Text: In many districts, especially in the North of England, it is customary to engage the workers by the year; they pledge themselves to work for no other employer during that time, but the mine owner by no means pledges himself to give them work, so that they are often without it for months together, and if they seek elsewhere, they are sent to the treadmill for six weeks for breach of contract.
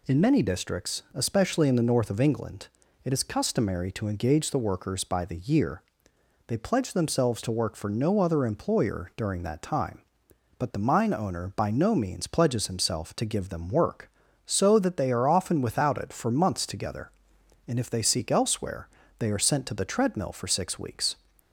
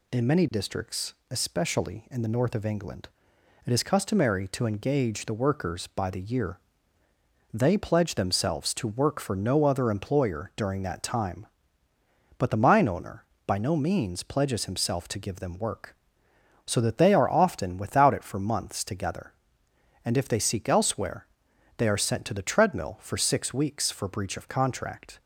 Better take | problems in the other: second | stops before "for breach of contract"; at 21.3 s

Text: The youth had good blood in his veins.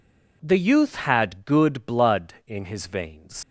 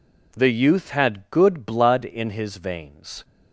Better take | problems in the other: second | leaves "veins" unfinished; at 3.4 s; 125 ms

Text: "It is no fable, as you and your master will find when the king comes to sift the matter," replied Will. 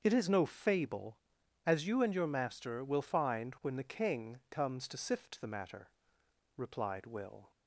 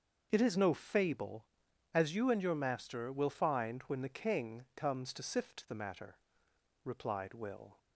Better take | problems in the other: neither | starts louder than the rest; the same in both

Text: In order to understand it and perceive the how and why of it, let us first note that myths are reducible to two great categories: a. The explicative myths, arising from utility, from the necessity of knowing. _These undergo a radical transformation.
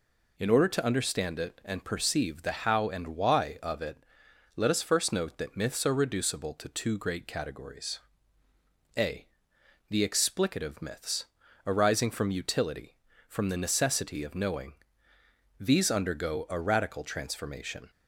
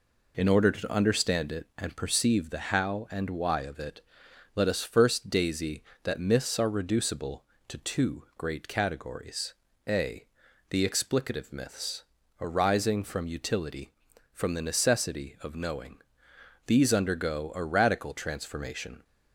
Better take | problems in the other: first | says "daisy" for "note"; at 5.2 s

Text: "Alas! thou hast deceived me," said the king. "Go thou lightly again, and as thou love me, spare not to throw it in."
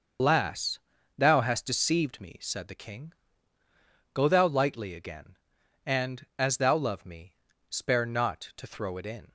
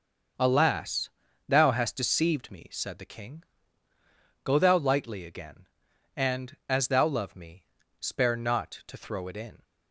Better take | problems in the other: second | loses the start of "Alas"; at 0.1 s; 135 ms // starts louder than the rest; until 1.5 s; 6.5 dB; also in the second

